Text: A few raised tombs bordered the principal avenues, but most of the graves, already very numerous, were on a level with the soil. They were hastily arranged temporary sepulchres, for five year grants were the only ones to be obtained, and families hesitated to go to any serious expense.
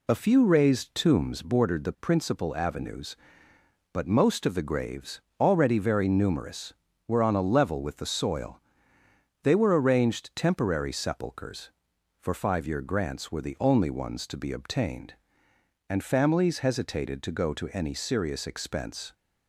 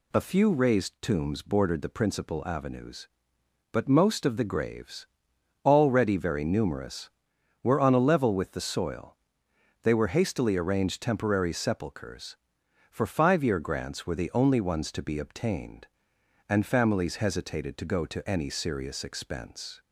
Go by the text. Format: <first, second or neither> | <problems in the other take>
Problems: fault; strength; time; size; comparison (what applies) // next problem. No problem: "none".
second | skips "hastily"; at 9.8 s